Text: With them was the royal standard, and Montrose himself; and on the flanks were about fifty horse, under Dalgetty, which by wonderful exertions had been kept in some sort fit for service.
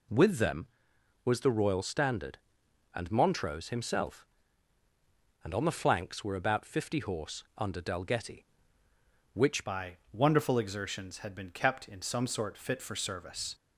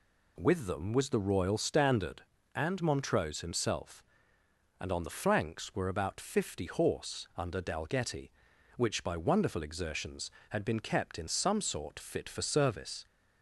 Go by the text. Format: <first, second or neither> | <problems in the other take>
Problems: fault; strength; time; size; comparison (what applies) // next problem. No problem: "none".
second | changes voice at "by"; from 9.6 s on; 3.9 s long // pauses between "by" and "wonderful"; slight; at 9.9 s; 0.20 s long